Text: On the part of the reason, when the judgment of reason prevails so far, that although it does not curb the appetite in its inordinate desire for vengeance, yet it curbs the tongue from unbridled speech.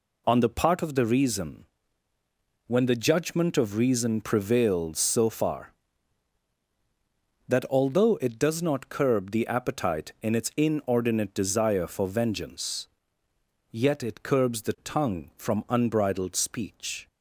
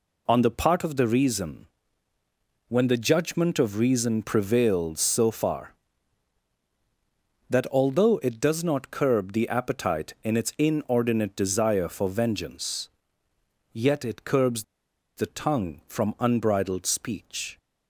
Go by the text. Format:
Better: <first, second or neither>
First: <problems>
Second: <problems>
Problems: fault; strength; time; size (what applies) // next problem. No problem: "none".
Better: first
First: none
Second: pauses between "curbs" and "the"; noticeable; at 14.6 s; 0.53 s long